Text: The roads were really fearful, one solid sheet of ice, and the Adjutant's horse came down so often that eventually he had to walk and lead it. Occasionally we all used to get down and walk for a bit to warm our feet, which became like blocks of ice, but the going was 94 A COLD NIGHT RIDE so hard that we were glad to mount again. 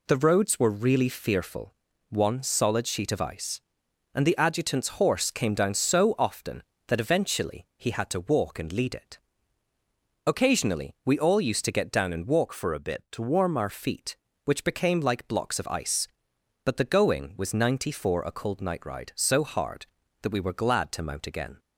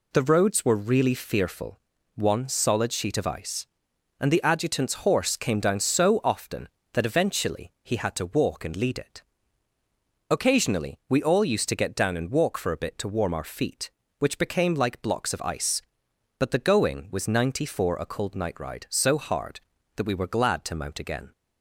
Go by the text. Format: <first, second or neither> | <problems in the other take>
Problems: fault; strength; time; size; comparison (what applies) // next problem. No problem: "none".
second | changes voice from "for" to "our"; from 12.5 to 13.6 s; 1.1 s long